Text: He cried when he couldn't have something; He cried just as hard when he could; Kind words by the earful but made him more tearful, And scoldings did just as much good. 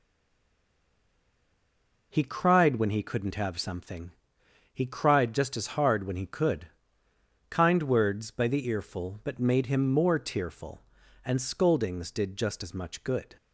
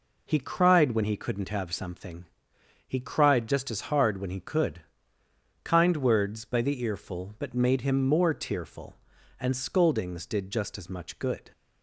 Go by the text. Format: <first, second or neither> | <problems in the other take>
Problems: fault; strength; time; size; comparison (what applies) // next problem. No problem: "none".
second | stays silent before the first word; until 2.1 s; 2.1 s long